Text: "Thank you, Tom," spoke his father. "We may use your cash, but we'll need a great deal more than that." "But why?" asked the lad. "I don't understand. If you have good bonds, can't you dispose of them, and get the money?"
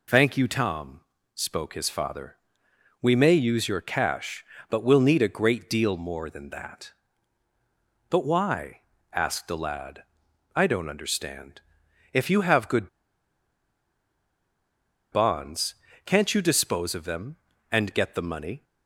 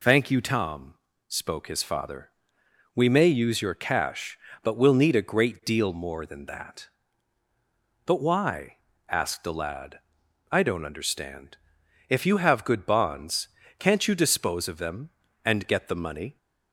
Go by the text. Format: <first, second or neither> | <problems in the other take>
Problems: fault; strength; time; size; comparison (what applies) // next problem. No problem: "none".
second | pauses between "good" and "bonds"; strong; at 12.8 s; 2.2 s long